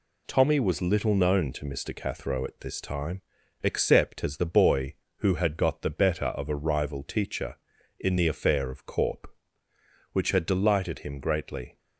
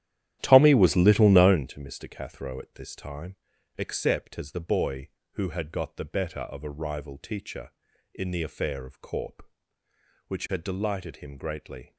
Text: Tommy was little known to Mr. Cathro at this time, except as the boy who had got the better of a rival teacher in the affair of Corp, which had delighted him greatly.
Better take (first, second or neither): first